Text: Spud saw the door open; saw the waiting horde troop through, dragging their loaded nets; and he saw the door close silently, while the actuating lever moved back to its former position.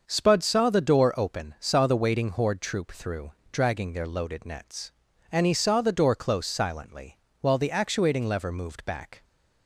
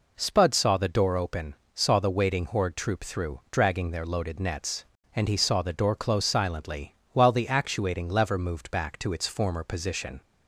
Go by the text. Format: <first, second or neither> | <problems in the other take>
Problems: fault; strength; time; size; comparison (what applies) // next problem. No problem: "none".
second | starts louder than the rest; until 1.0 s; 6.5 dB // stops before "to its former position"; at 9.2 s